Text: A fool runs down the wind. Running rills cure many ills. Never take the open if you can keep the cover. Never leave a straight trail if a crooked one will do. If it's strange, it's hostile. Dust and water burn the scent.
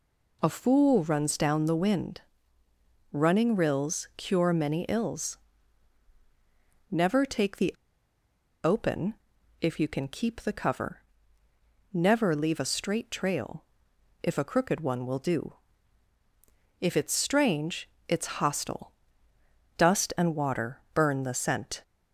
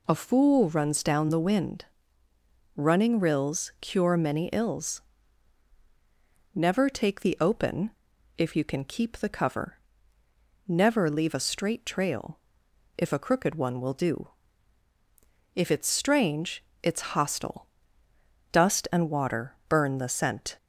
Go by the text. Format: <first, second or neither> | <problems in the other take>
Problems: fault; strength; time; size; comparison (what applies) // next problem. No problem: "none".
second | pauses between "the" and "open"; noticeable; at 7.7 s; 0.90 s long // pauses between "open" and "if"; noticeable; at 9.1 s; 0.46 s long; noticeable in the second // pauses between "trail" and "if"; noticeable; at 13.6 s; 0.58 s long; noticeable in the second // pauses between "water" and "burn"; slight; at 20.7 s; 0.16 s long; slight in the second